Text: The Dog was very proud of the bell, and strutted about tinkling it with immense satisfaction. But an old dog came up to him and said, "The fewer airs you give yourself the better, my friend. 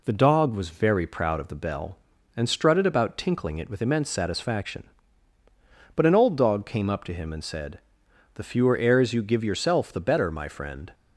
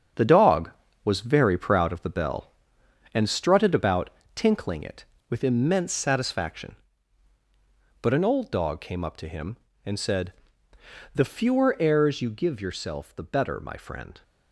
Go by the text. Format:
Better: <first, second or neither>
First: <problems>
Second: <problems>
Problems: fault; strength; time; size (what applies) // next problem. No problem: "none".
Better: first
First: none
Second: gets quieter; strong; throughout; 8 dB // pauses between "about" and "tinkling"; slight; at 4.0 s; 0.26 s long